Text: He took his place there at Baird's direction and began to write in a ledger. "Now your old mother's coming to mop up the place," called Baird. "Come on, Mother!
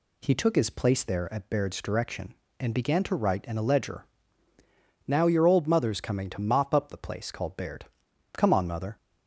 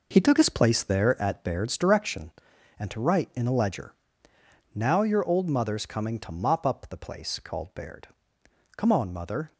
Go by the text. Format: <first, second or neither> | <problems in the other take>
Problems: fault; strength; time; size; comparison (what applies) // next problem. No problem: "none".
first | skips "began"; at 2.9 s